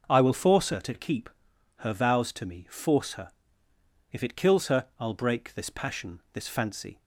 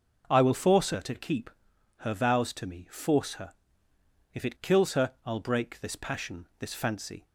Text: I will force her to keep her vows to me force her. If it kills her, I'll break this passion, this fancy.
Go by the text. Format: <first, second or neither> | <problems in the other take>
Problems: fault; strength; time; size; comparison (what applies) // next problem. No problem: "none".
neither | pauses between "keep" and "her"; noticeable; the same in both